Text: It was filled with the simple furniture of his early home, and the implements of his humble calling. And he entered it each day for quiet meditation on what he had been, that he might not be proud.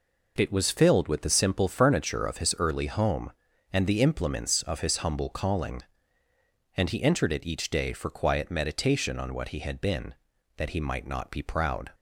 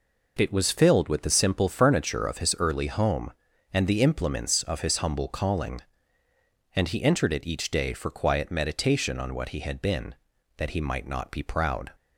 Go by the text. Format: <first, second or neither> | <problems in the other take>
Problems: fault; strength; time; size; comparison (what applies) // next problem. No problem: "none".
neither | none